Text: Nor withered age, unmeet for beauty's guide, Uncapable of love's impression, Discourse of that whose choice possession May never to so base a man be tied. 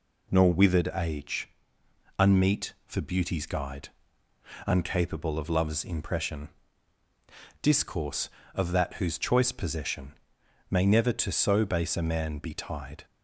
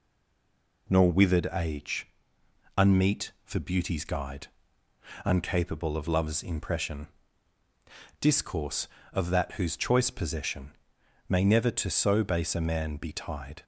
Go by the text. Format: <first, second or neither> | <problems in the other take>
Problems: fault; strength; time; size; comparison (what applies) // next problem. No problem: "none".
first | stays silent before the first word; slight; until 0.8 s; 0.8 s long // pauses between "possession" and "May"; noticeable; at 10.7 s; 0.56 s long; noticeable in the first